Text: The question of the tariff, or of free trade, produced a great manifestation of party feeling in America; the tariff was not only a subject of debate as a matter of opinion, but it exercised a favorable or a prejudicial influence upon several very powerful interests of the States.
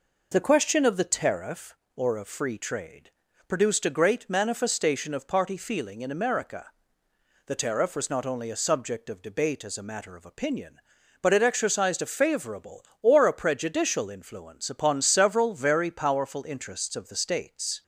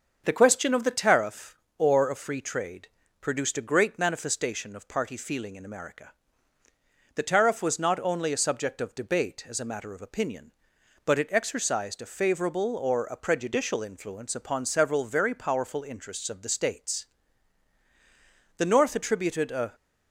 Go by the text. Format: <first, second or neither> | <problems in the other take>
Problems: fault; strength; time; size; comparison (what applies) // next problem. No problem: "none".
first | starts louder than the rest; until 1.2 s; 6.5 dB // goes on to say "The North attributed a"; noticeable; from 18.5 s on; 1.1 s long